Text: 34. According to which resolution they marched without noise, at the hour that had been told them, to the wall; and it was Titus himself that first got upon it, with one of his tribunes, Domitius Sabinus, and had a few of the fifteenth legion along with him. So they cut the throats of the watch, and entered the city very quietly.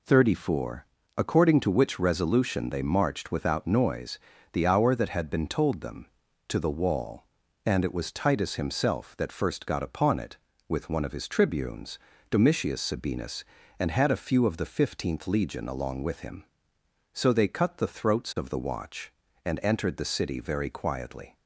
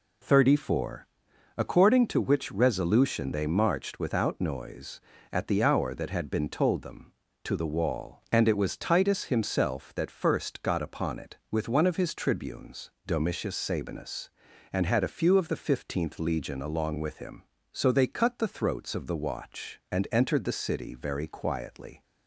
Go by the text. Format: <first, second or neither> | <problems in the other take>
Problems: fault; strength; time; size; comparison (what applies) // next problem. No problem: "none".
second | skips "at"; at 4.3 s